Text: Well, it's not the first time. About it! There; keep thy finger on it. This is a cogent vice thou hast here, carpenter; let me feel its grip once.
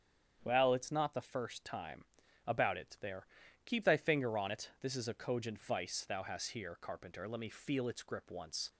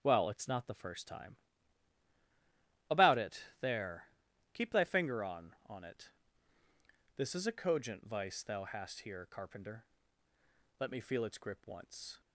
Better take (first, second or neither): first